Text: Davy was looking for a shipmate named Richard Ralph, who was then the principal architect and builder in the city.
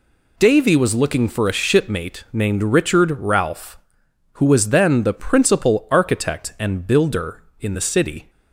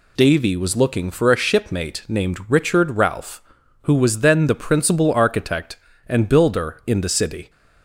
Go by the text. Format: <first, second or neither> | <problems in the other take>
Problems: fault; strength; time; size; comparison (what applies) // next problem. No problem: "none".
neither | none